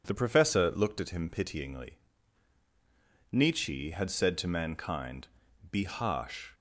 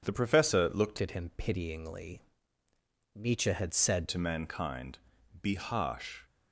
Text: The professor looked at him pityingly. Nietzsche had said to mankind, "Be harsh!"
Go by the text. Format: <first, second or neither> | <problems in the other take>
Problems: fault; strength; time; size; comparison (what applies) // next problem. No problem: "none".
first | changes voice from "at" to "said"; from 0.9 to 4.0 s; 3.1 s long